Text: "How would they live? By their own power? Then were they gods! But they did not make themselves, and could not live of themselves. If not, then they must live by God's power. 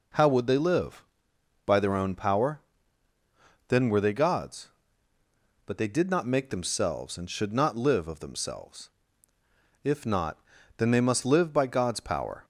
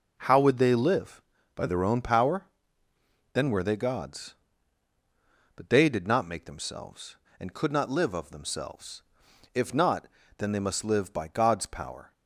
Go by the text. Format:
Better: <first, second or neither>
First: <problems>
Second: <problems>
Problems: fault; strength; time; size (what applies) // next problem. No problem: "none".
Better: second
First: says "should" for "could"; at 7.3 s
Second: none